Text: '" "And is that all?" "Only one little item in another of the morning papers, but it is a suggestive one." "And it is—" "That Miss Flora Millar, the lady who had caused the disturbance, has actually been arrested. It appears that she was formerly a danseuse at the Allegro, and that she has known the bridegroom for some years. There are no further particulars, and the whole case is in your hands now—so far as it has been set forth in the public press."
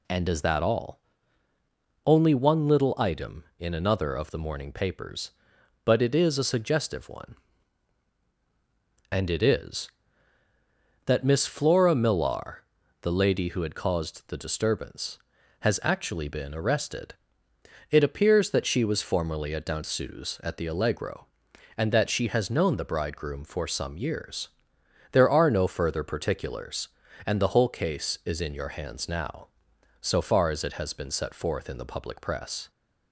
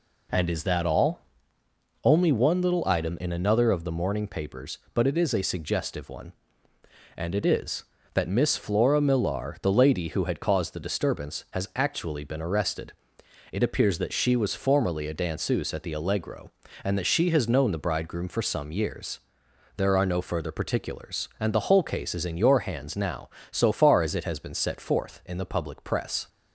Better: neither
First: none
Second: none

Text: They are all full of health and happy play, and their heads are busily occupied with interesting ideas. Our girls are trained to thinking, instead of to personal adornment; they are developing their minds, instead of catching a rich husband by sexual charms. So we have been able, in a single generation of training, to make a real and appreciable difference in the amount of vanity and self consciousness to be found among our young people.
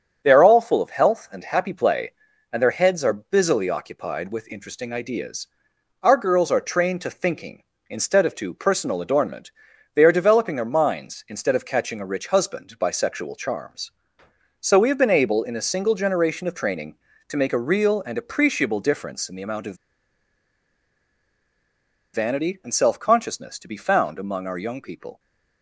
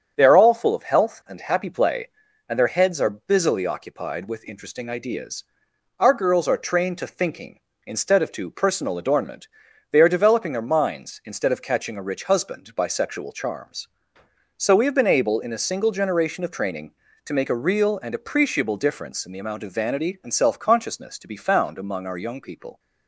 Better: second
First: starts louder than the rest; strong; until 1.2 s; 8 dB // pauses between "of" and "vanity"; strong; at 19.7 s; 2.3 s long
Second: starts louder than the rest; strong; until 1.1 s; 8 dB

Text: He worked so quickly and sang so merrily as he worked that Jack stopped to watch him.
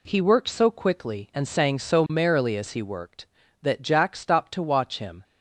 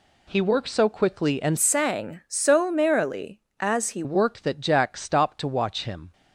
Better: first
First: none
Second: changes voice from "sang" to "he"; from 1.5 to 4.0 s; 2.5 s long

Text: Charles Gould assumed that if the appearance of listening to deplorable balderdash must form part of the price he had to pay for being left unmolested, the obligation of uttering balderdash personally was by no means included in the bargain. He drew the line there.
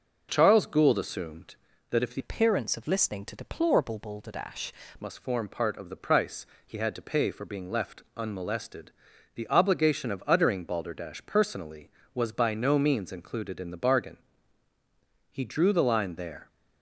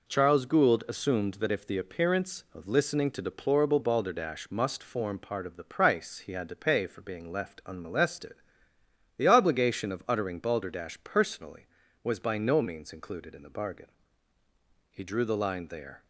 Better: second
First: changes voice from "appearance" to "balderdash"; from 2.1 to 4.7 s; 2.6 s long // pauses between "price" and "he"; slight; at 6.4 s; 0.18 s long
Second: none

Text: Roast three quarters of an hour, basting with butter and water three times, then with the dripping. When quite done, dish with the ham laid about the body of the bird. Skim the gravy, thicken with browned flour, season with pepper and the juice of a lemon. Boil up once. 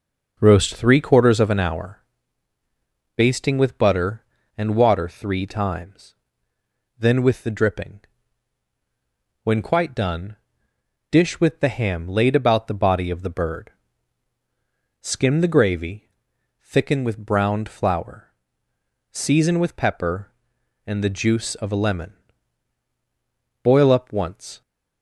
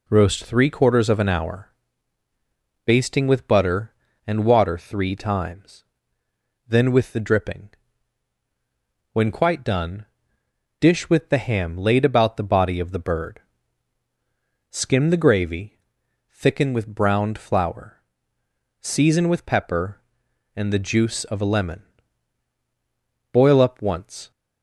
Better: second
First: starts louder than the rest; noticeable; until 1.6 s; 5 dB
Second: none

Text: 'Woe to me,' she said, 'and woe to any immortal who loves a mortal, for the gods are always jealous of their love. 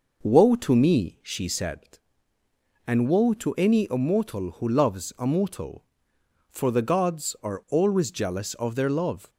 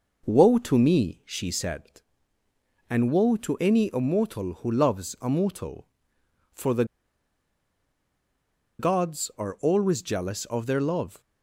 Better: first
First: none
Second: pauses between "the" and "gods"; strong; at 6.8 s; 1.9 s long

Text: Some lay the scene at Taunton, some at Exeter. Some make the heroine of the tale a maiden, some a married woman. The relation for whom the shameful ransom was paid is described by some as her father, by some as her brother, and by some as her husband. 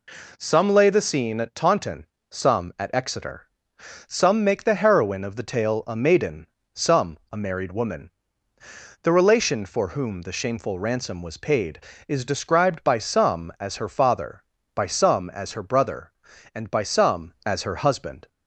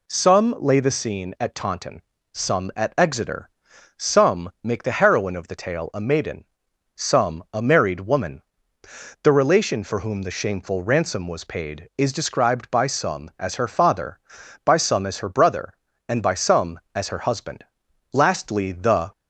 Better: first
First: none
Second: goes on to say "Lastly the"; noticeable; from 18.1 s on; 0.98 s long

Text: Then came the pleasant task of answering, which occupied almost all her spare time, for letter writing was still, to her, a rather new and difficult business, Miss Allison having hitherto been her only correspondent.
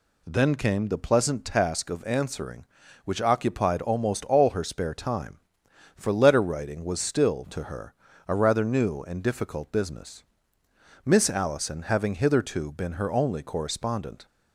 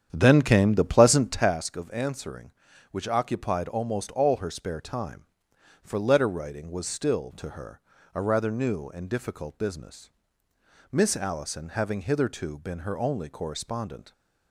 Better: first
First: none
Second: starts louder than the rest; strong; until 1.6 s; 9 dB

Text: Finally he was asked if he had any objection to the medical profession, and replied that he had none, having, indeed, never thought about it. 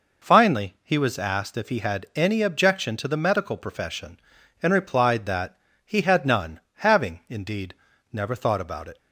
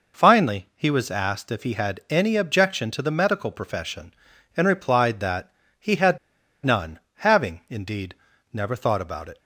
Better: first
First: pauses between "that" and "he"; slight; at 5.5 s; 0.26 s long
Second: pauses between "that" and "he"; slight; at 5.5 s; 0.26 s long // pauses between "had" and "none"; noticeable; at 6.1 s; 0.48 s long

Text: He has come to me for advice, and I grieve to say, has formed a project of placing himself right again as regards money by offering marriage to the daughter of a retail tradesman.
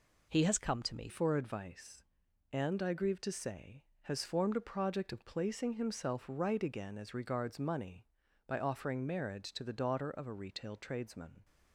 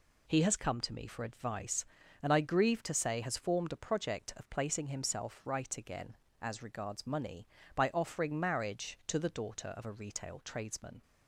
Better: second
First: changes voice at "for"; from 1.0 s on; 10.4 s long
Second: none

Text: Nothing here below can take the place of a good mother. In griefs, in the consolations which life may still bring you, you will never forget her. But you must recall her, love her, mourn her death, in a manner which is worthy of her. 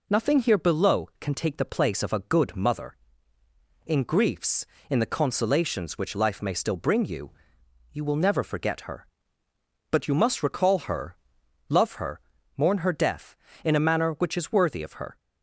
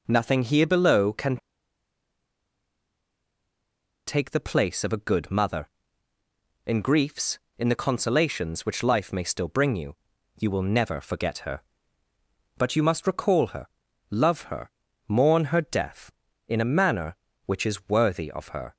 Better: first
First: none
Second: pauses between "can" and "take"; strong; at 1.3 s; 2.7 s long

